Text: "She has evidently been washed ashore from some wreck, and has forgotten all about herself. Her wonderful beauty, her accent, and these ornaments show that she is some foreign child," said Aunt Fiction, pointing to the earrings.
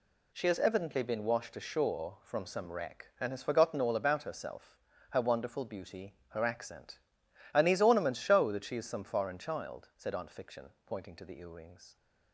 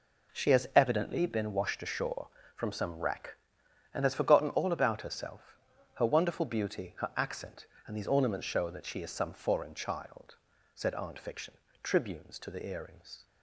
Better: first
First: none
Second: says "tribunes" for "pointing"; at 11.8 s

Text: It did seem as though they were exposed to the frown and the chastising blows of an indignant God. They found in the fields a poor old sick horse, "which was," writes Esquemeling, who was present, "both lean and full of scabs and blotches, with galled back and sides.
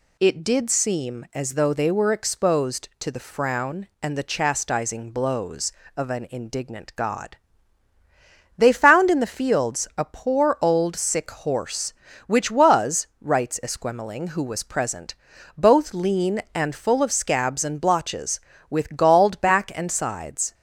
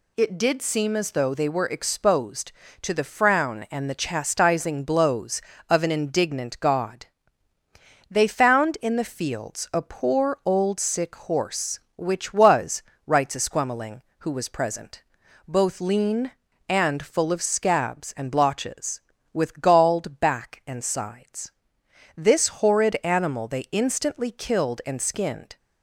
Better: first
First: none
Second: goes on to say "This horrid animal they instantly killed and skinned"; strong; from 22.1 s on; 3.4 s long

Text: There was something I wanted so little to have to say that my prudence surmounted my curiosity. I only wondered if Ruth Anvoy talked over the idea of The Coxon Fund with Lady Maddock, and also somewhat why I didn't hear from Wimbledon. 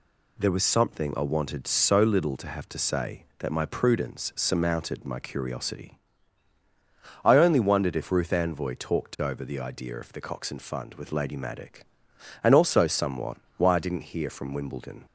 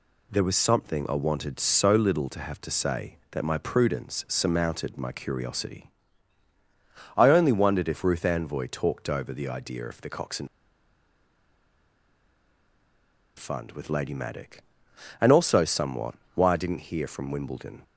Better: first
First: pauses between "somewhat" and "why"; slight; at 13.3 s; 0.20 s long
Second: pauses between "Coxon" and "Fund"; strong; at 10.4 s; 2.9 s long // pauses between "somewhat" and "why"; slight; at 16.1 s; 0.20 s long

